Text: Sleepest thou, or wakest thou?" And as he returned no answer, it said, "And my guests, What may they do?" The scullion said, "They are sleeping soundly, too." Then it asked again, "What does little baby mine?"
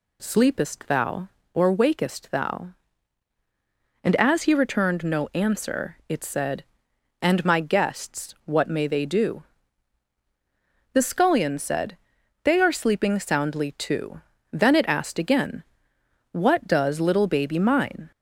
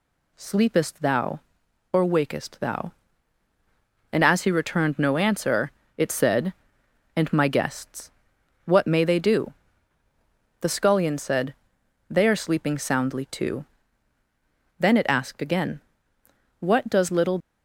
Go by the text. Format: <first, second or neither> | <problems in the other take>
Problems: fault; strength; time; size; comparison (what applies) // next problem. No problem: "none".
first | stops before "baby mine"; at 17.4 s